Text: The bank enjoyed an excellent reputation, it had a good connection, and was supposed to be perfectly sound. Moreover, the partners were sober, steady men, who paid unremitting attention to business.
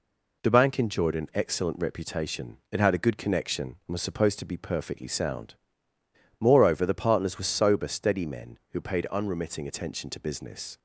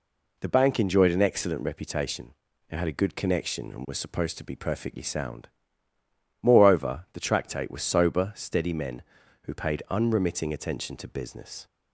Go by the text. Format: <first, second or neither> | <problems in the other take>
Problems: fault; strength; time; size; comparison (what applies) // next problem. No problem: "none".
first | says "tractate" for "partners"; at 7.1 s